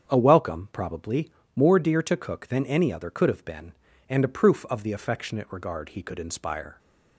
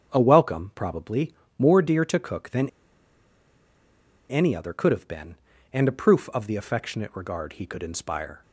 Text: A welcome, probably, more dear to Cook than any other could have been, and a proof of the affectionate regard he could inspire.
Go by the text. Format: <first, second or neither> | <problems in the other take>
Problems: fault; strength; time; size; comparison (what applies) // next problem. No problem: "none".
first | starts louder than the rest; strong; until 1.1 s; 7.5 dB; strong in the first // pauses between "than" and "any"; strong; at 2.6 s; 1.6 s long